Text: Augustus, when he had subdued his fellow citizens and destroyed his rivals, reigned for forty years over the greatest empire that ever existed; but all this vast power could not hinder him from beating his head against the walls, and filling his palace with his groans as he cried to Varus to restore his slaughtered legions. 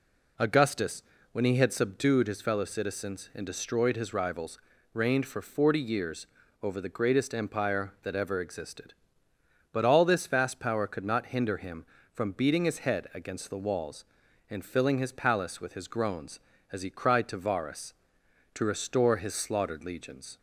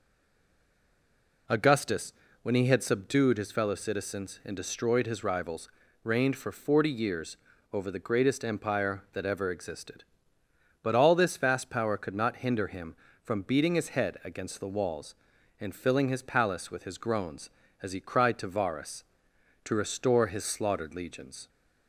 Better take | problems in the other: first | stays silent before the first word; noticeable; until 1.4 s; 1.4 s long // pauses between "years" and "over"; slight; at 7.3 s; 0.36 s long; slight in the first

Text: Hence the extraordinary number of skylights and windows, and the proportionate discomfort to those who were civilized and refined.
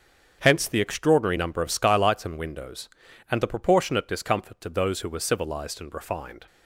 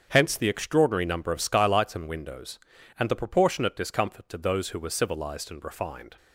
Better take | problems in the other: neither | starts louder than the rest; strong; the same in both

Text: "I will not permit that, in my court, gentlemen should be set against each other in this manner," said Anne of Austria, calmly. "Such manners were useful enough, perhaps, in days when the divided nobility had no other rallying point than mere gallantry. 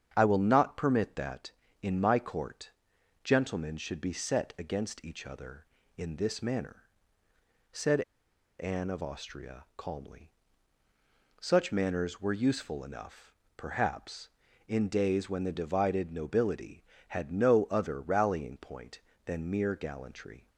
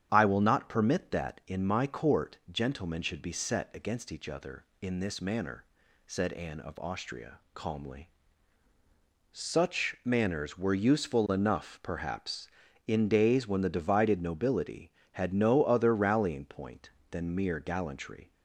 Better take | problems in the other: second | starts louder than the rest; strong; until 1.1 s; 8 dB; strong in the second // pauses between "said" and "Anne"; noticeable; at 8.0 s; 0.56 s long

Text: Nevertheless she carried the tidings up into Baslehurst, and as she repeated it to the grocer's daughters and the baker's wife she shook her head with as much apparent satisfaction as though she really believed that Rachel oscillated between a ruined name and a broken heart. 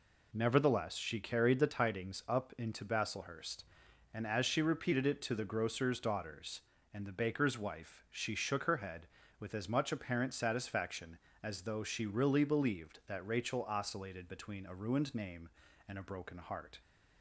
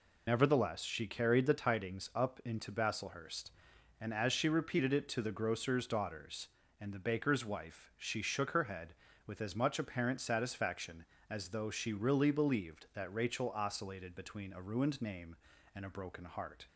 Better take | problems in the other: first | loses the start of "Nevertheless"; at 0.2 s; 75 ms

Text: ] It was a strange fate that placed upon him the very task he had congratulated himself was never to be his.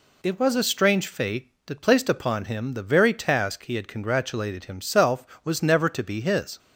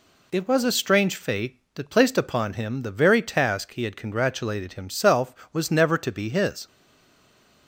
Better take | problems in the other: first | stays silent after the last word; from 6.6 s on; 1.0 s long

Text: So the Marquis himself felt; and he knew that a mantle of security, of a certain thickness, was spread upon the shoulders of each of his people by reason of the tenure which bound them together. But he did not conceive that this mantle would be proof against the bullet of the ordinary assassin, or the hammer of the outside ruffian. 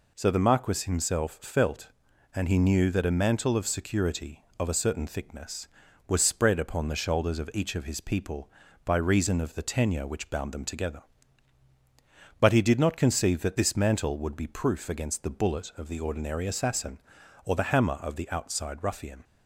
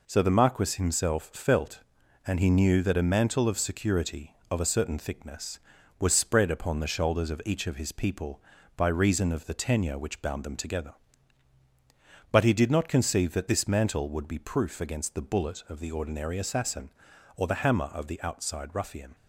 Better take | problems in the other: first | gets quieter; noticeable; throughout; 5.5 dB

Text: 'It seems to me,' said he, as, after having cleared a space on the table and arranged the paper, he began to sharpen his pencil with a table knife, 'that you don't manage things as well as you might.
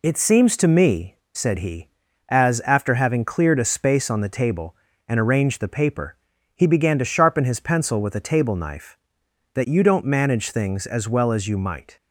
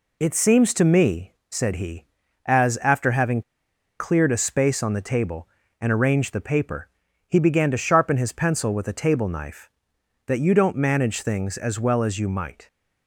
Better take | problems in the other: first | pauses between "having" and "cleared"; noticeable; at 3.4 s; 0.57 s long

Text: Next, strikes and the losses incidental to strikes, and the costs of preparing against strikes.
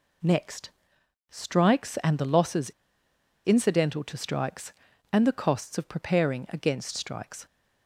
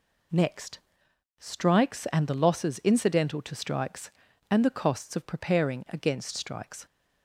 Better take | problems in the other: second | pauses between "losses" and "incidental"; noticeable; at 2.7 s; 0.74 s long

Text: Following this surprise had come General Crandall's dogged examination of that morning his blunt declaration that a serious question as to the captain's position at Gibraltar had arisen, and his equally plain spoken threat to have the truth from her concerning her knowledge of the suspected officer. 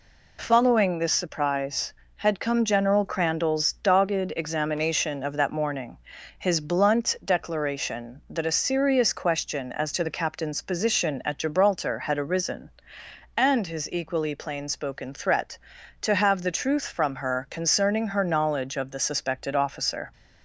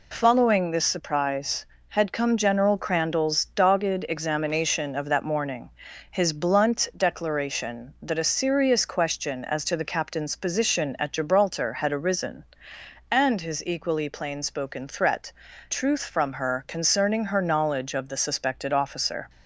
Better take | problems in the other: first | pauses between "morning" and "his"; at 5.6 s; 0.40 s long; also in the first // skips "to have the"; at 15.5 s

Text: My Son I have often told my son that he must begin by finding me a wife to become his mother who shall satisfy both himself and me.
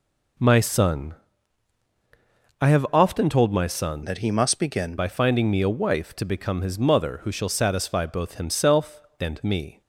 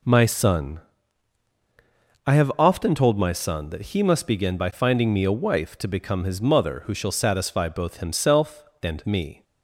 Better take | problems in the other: second | pauses between "Son" and "I"; strong; at 1.1 s; 1.4 s long; strong in the second // changes voice from "that" to "begin"; from 4.0 to 4.9 s; 0.9 s long

